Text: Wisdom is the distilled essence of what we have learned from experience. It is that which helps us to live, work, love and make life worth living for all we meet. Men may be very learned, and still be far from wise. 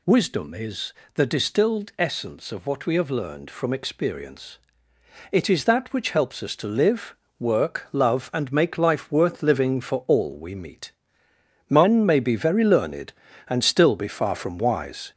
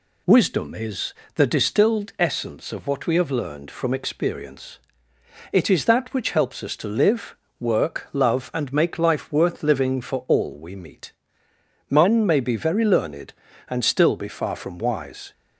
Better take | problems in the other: second | gets louder; noticeable; throughout; 4.5 dB // pauses between "is" and "the"; slight; at 0.9 s; 0.22 s long; slight in the second

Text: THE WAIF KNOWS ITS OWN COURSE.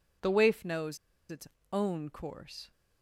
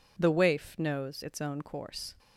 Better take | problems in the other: second | pauses between "KNOWS" and "ITS"; slight; at 0.9 s; 0.33 s long // pauses between "ITS" and "OWN"; slight; at 1.4 s; 0.24 s long

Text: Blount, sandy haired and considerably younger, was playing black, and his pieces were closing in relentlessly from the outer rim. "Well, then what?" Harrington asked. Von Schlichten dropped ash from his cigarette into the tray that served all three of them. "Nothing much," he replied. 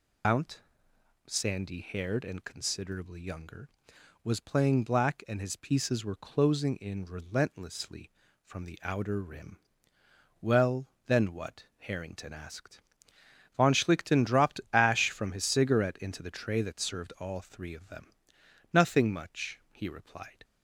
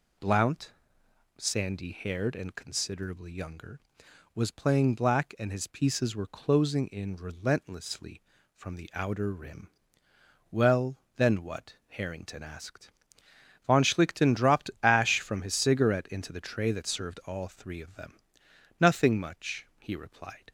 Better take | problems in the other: second | loses the start of "Blount"; at 0.2 s; 160 ms

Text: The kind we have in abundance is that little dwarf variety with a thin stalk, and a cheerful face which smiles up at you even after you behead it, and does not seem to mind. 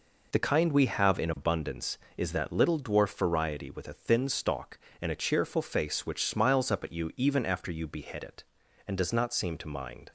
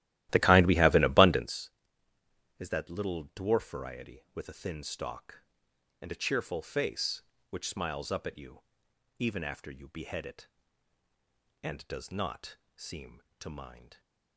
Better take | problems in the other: first | starts louder than the rest; strong; until 1.6 s; 15 dB // pauses between "you" and "even"; noticeable; at 8.6 s; 0.58 s long // pauses between "not" and "seem"; slight; at 12.5 s; 0.20 s long

